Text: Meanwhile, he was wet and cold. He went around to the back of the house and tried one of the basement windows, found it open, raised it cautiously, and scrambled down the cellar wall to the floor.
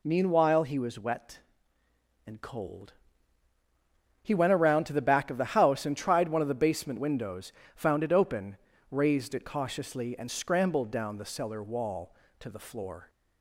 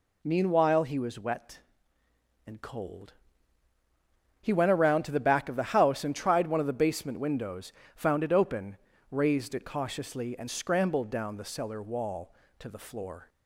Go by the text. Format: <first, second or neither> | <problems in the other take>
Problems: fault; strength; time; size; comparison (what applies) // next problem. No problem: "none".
neither | none